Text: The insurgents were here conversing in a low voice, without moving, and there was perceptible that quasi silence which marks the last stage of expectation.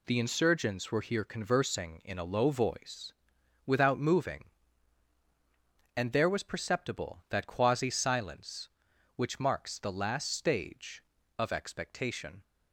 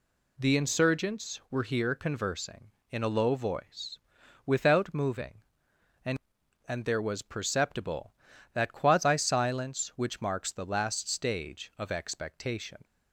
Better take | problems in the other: first | says "and" twice; at 6.6 s

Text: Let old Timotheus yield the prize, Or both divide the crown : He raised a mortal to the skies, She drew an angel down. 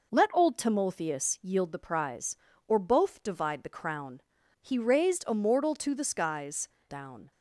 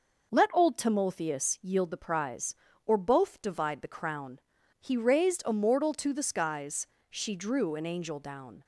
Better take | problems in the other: second | skips "She drew an angel"; at 6.7 s

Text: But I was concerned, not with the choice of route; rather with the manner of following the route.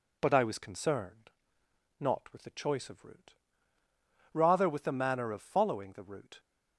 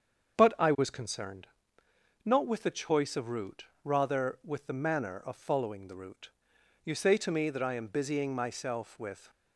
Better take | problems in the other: first | starts louder than the rest; strong; until 2.2 s; 7 dB // goes on to say "You say to me that I am busying myself with"; strong; from 6.8 s on; 2.4 s long

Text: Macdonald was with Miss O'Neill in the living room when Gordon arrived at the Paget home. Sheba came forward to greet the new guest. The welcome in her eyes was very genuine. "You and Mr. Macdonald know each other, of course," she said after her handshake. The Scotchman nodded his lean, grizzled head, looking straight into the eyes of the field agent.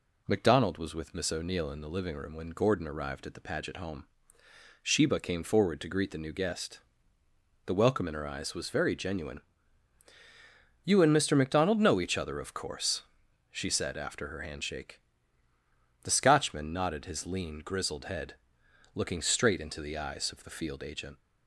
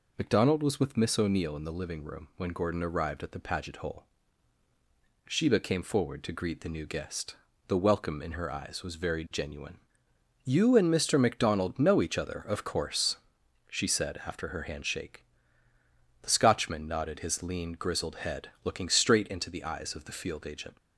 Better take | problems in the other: first | says "hole" for "home"; at 3.7 s

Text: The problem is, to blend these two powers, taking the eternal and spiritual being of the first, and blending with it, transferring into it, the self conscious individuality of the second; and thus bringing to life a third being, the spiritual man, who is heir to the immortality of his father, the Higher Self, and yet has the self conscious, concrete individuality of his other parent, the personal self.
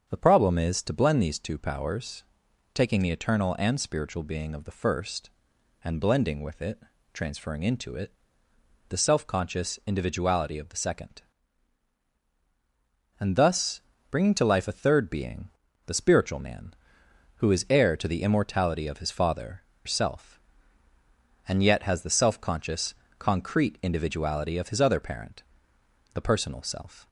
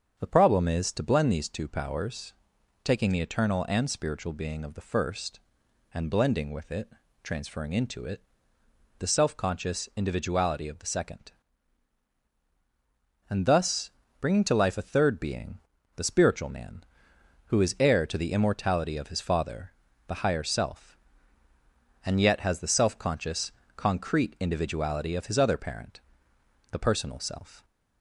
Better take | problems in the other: second | starts louder than the rest; strong; until 1.1 s; 7 dB; strong in the second // pauses between "thus" and "bringing"; slight; at 13.7 s; 0.32 s long; slight in the second // skips "the Higher"; at 19.7 s

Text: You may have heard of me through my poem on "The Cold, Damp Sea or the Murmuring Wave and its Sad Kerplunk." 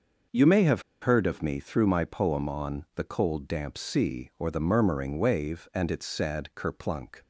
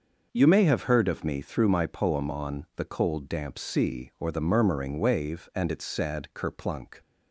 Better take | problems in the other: second | starts louder than the rest; noticeable; until 1.5 s; 6 dB; noticeable in the second // pauses between "have" and "heard"; slight; at 0.8 s; 0.19 s long

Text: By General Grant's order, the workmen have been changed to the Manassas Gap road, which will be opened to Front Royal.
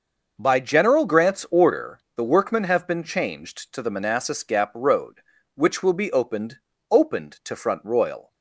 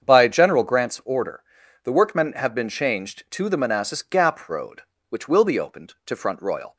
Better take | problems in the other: second | starts louder than the rest; noticeable; until 1.3 s; 6 dB; strong in the second // says "opened" twice; at 6.9 s

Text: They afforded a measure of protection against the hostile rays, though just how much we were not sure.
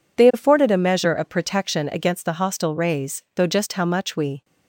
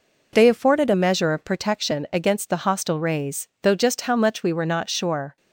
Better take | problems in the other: second | stops before "were not sure"; at 4.4 s

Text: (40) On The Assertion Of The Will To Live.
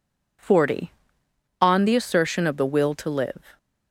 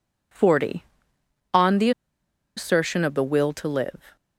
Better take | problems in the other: first | pauses between "The" and "Assertion"; noticeable; at 1.9 s; 0.66 s long

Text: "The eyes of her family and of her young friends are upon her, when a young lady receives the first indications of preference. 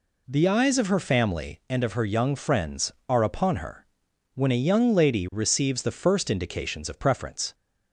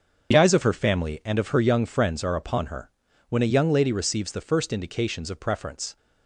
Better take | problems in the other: first | loses the start of "The"; at 0.3 s; 25 ms // starts louder than the rest; until 1.3 s; 7 dB

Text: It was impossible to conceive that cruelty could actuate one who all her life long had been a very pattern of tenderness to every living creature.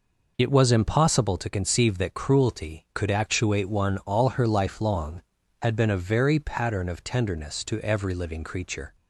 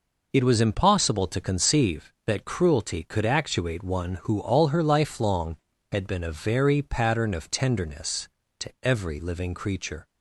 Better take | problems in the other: second | skips "who"; at 3.9 s

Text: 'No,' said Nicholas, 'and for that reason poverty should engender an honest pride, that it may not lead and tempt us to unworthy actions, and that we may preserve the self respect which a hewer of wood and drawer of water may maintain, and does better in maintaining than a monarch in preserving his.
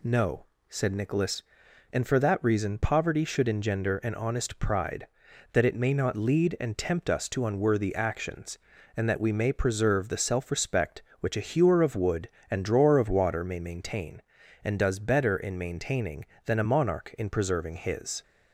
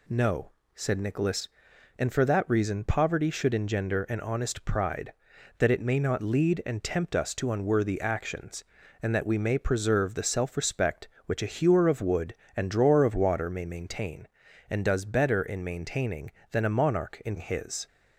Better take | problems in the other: first | skips "preserving"; at 17.3 s

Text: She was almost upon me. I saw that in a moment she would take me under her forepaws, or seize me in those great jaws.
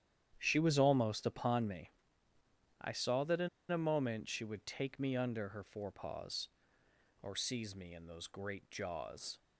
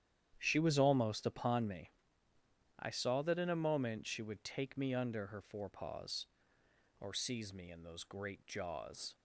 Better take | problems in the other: second | starts louder than the rest; strong; until 1.3 s; 10 dB; strong in the second // pauses between "in" and "a"; slight; at 3.4 s; 0.21 s long

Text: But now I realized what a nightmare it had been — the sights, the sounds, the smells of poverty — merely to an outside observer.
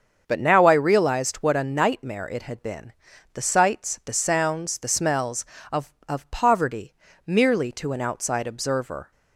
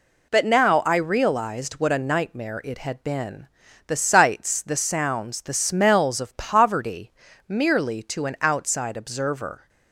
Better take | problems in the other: second | starts louder than the rest; until 1.2 s; 7 dB // says "of" twice; at 6.0 s

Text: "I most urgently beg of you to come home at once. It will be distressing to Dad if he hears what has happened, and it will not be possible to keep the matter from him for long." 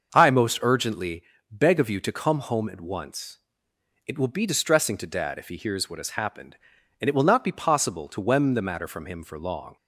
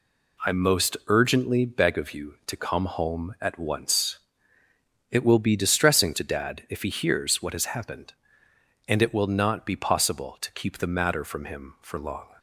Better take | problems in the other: second | starts louder than the rest; until 1.1 s; 6.5 dB // pauses between "urgently" and "beg"; slight; at 1.2 s; 0.30 s long // says "wem" for "keep"; at 8.1 s

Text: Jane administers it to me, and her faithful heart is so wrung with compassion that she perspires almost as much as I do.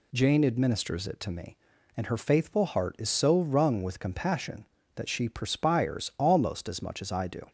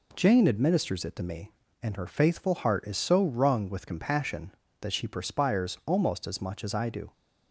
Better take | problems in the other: neither | none

